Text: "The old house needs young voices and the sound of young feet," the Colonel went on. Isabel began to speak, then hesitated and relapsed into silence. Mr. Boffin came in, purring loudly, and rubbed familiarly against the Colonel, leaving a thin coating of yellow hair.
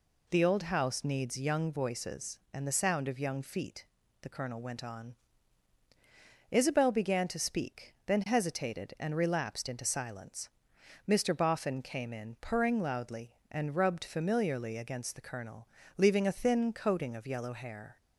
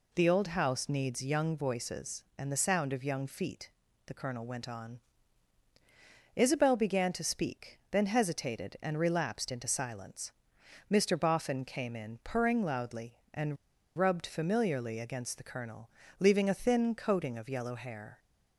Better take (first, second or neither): first